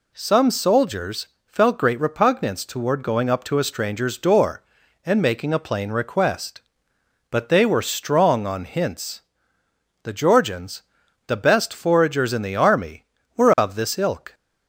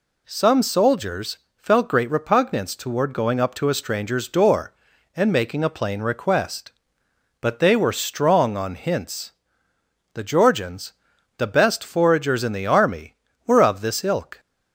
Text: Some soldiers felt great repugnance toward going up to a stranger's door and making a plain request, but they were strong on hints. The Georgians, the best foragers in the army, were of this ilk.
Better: neither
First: pauses between "soldiers" and "felt"; slight; at 1.2 s; 0.22 s long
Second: pauses between "soldiers" and "felt"; slight; at 1.3 s; 0.22 s long

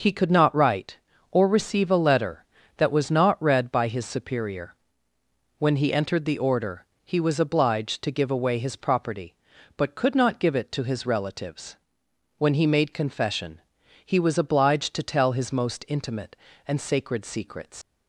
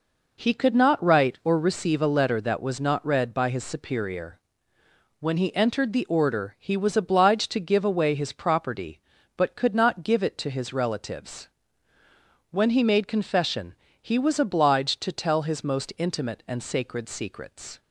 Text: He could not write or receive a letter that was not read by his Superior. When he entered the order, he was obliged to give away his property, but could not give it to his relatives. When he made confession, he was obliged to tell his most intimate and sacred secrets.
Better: second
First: leaves "secrets" unfinished; at 17.8 s; 95 ms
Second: none

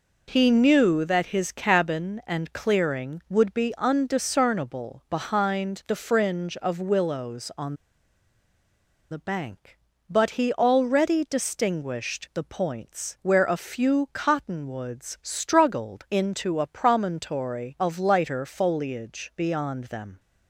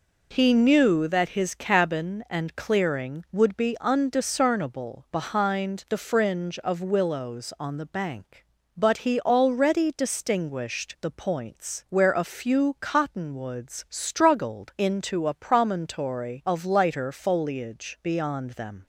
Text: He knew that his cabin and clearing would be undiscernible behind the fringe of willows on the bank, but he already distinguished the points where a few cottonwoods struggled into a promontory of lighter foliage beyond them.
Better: second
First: pauses between "on" and "the"; strong; at 7.7 s; 1.3 s long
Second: none

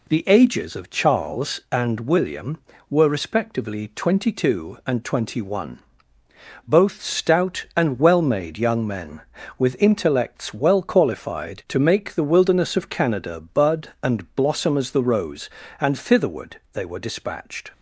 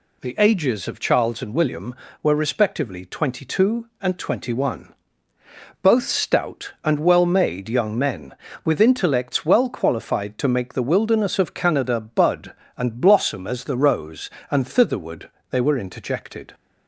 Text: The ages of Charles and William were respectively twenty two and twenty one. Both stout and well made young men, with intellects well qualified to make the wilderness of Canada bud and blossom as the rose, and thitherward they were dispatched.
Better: first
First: none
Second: pauses between "thitherward" and "they"; slight; at 15.3 s; 0.20 s long // says "interjected" for "dispatched"; at 15.7 s

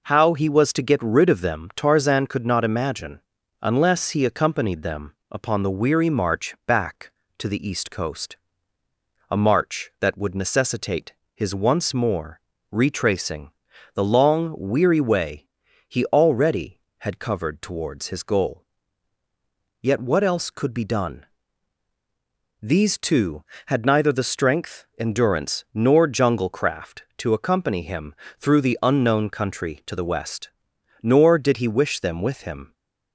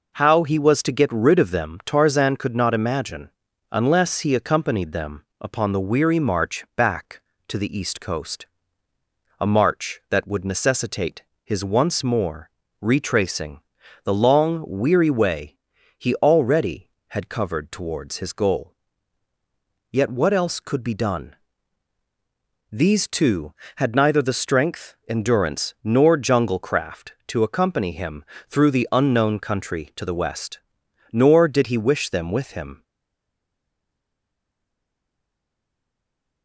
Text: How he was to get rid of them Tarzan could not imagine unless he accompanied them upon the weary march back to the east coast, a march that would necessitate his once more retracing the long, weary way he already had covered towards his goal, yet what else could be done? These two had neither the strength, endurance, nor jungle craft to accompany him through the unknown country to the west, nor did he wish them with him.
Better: first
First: pauses between "imagine" and "unless"; at 3.2 s; 0.40 s long // pauses between "them" and "upon"; slight; at 5.1 s; 0.18 s long // pauses between "necessitate" and "his"; slight; at 11.1 s; 0.20 s long // pauses between "more" and "retracing"; slight; at 12.4 s; 0.28 s long // pauses between "retracing" and "the"; at 13.5 s; 0.42 s long // pauses between "way" and "he"; at 15.4 s; 0.40 s long // pauses between "him" and "through"; slight; at 28.1 s; 0.24 s long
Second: pauses between "imagine" and "unless"; at 3.3 s; 0.40 s long // pauses between "them" and "upon"; slight; at 5.2 s; 0.18 s long // pauses between "necessitate" and "his"; slight; at 11.2 s; 0.20 s long // pauses between "more" and "retracing"; slight; at 12.5 s; 0.28 s long // pauses between "retracing" and "the"; at 13.6 s; 0.42 s long // pauses between "way" and "he"; at 15.5 s; 0.40 s long // pauses between "him" and "through"; slight; at 28.2 s; 0.24 s long // stays silent after the last word; strong; from 32.8 s on; 3.6 s long

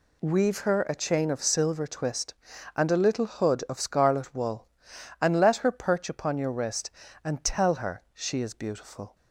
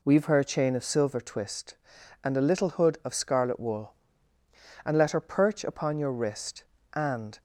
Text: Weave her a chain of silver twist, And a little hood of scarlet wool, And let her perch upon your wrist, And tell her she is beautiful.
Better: first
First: none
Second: stops before "tell her she is beautiful"; at 7.3 s

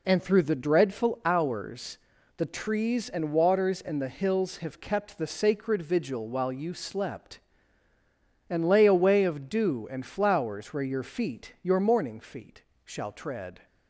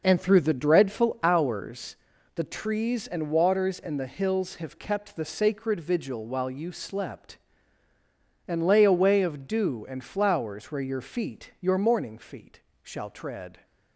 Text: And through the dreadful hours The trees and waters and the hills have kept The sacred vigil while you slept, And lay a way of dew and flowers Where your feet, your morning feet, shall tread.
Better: first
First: pauses between "hours" and "The"; at 1.9 s; 0.40 s long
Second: starts louder than the rest; noticeable; until 1.9 s; 5.5 dB // pauses between "hours" and "The"; at 1.9 s; 0.40 s long

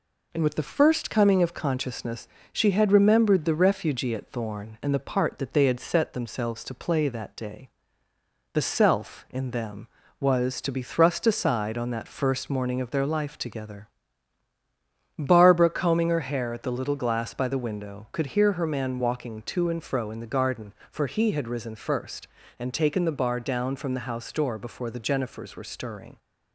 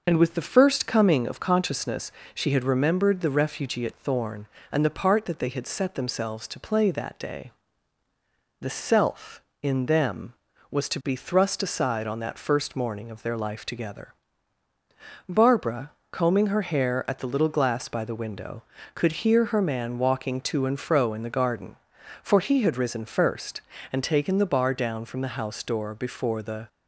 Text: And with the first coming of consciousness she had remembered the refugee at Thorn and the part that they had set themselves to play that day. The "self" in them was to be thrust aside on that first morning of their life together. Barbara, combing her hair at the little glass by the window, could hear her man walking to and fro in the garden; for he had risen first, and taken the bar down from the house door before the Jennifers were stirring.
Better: first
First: pauses between "consciousness" and "she"; slight; at 2.2 s; 0.24 s long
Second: pauses between "consciousness" and "she"; slight; at 2.1 s; 0.24 s long // stops before "Jennifers were stirring"; at 26.6 s

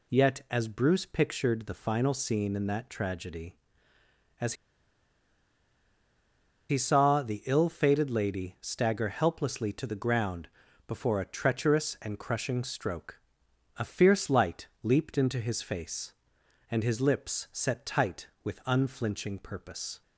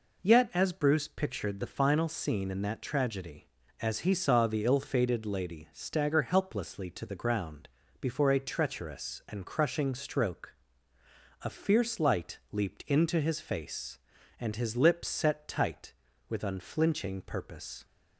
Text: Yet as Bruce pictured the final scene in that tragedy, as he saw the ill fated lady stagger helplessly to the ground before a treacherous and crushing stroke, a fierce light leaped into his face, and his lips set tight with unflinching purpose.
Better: second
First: pauses between "as" and "he"; strong; at 4.5 s; 2.1 s long // pauses between "ground" and "before"; at 10.4 s; 0.38 s long // pauses between "light" and "leaped"; slight; at 14.6 s; 0.16 s long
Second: pauses between "ground" and "before"; slight; at 7.6 s; 0.32 s long

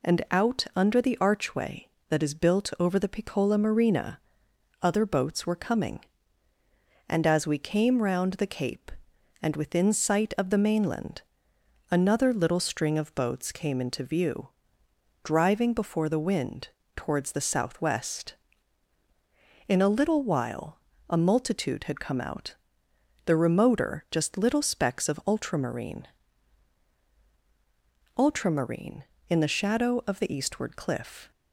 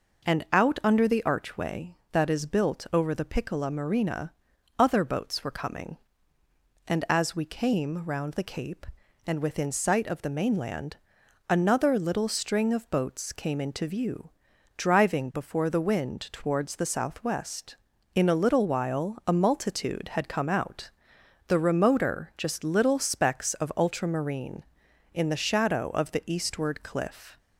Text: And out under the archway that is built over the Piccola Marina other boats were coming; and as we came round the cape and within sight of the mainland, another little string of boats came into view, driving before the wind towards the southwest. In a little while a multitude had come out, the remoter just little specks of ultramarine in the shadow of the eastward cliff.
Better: second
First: pauses between "Marina" and "other"; noticeable; at 4.1 s; 0.64 s long // pauses between "wind" and "towards"; slight; at 16.6 s; 0.26 s long // pauses between "while" and "a"; slight; at 20.7 s; 0.32 s long // says "ultramarine" twice; at 28.1 s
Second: pauses between "Marina" and "other"; noticeable; at 4.3 s; 0.48 s long

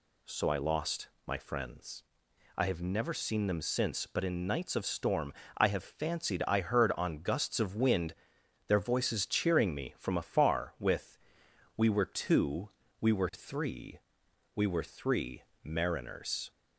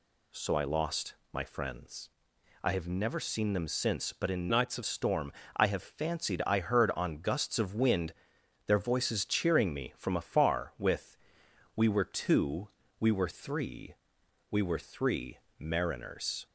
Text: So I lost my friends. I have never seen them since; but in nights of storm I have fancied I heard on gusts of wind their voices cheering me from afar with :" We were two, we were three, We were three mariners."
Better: first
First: pauses between "lost" and "my"; slight; at 1.0 s; 0.18 s long // pauses between "storm" and "I"; slight; at 5.3 s; 0.24 s long // pauses between "wind" and "their"; noticeable; at 8.1 s; 0.54 s long // pauses between "three" and "mariners"; slight; at 15.4 s; 0.18 s long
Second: pauses between "lost" and "my"; slight; at 1.1 s; 0.18 s long // changes voice from "nights" to "of"; from 4.4 to 4.8 s; 0.4 s long // pauses between "storm" and "I"; slight; at 5.3 s; 0.24 s long // pauses between "wind" and "their"; noticeable; at 8.1 s; 0.54 s long // pauses between "three" and "mariners"; slight; at 15.3 s; 0.18 s long

